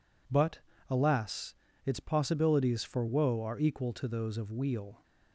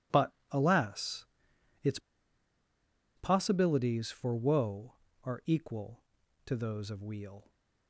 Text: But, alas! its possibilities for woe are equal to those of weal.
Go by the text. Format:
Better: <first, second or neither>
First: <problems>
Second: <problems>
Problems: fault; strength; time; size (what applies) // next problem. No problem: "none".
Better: first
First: none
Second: pauses between "its" and "possibilities"; at 1.9 s; 1.1 s long